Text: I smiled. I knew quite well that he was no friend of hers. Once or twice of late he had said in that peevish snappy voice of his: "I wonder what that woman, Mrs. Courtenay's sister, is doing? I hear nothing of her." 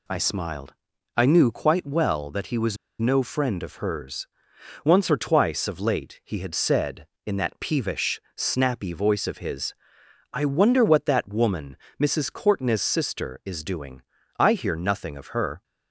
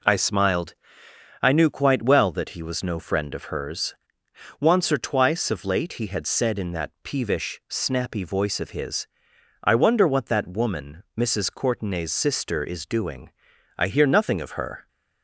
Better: second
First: pauses between "was" and "no"; slight; at 2.7 s; 0.24 s long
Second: none

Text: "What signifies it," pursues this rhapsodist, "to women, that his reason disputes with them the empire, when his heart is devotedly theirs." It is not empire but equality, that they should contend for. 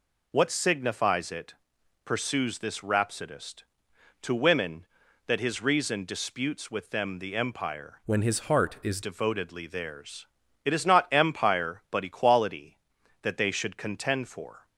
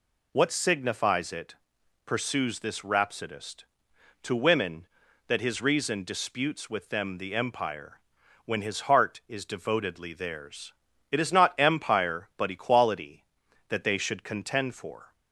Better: second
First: changes voice from "when" to "is"; from 8.0 to 9.0 s; 1.0 s long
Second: none

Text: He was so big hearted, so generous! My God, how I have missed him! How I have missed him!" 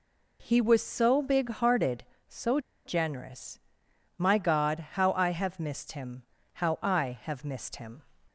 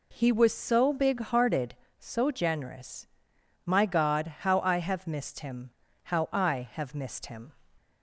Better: second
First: pauses between "so" and "generous"; slight; at 2.5 s; 0.26 s long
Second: none

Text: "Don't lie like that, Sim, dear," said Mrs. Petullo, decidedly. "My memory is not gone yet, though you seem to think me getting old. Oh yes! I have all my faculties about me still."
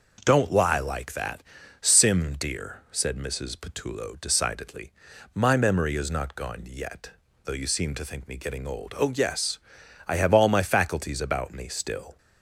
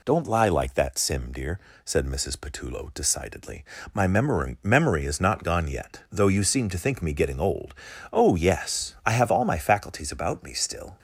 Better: first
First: none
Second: says "memory" twice; at 4.6 s

